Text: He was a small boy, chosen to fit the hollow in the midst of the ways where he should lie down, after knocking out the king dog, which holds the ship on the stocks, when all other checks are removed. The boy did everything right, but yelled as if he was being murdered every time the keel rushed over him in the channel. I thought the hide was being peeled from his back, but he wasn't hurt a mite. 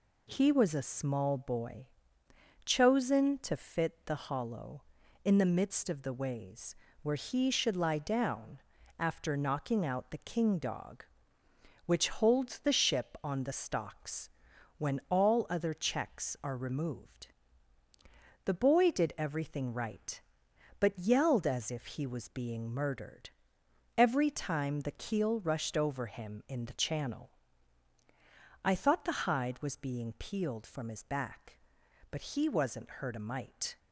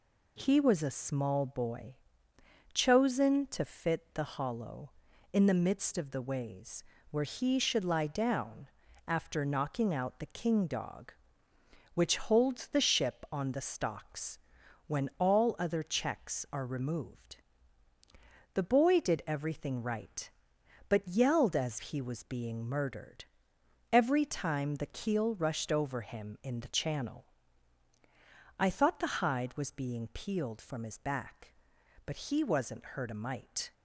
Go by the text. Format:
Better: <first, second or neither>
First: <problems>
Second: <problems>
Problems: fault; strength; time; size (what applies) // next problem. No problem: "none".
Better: first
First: pauses between "ways" and "where"; slight; at 6.7 s; 0.26 s long // pauses between "murdered" and "every"; noticeable; at 23.2 s; 0.66 s long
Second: pauses between "ways" and "where"; slight; at 6.8 s; 0.26 s long // skips "if"; at 21.7 s // pauses between "murdered" and "every"; noticeable; at 23.2 s; 0.66 s long